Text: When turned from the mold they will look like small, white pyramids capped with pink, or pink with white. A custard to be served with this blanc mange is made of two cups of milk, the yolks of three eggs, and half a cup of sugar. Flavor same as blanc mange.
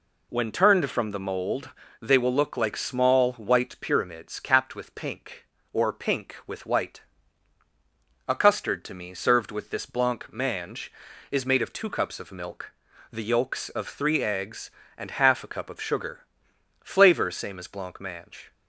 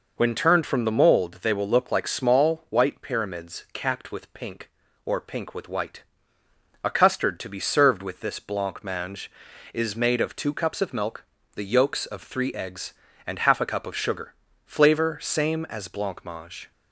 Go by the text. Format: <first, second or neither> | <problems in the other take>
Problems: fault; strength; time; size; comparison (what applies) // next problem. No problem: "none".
second | pauses between "mold" and "they"; slight; at 1.6 s; 0.30 s long // says "me" for "be"; at 8.9 s